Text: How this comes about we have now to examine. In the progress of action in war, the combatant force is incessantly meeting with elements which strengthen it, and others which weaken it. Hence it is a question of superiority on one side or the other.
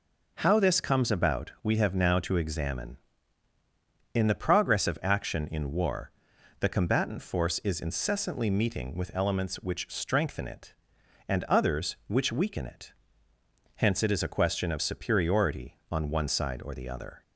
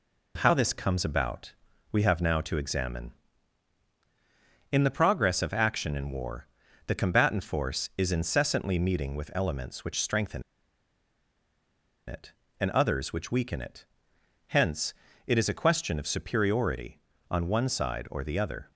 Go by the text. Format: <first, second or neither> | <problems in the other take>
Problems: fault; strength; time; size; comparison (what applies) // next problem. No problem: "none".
first | pauses between "about" and "we"; slight; at 1.5 s; 0.36 s long // pauses between "strengthen" and "it"; strong; at 10.4 s; 1.6 s long // pauses between "Hence" and "it"; slight; at 14.9 s; 0.32 s long